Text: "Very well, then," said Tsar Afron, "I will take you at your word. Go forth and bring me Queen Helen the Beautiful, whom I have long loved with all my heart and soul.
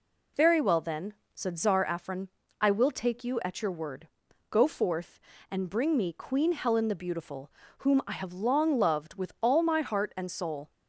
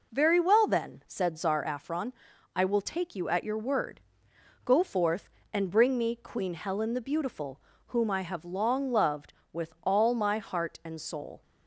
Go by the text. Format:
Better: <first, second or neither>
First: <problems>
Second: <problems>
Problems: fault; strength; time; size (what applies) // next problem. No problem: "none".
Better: first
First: none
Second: starts louder than the rest; noticeable; until 1.9 s; 4.5 dB